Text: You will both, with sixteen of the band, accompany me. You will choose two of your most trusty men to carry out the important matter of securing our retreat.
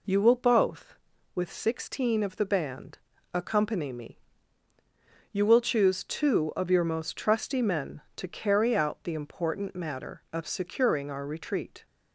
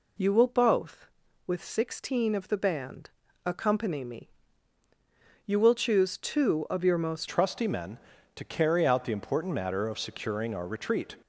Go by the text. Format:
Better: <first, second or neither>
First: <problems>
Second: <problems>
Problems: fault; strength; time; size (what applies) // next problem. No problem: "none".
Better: first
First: none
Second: changes voice at "trusty"; from 7.2 s on; 3.9 s long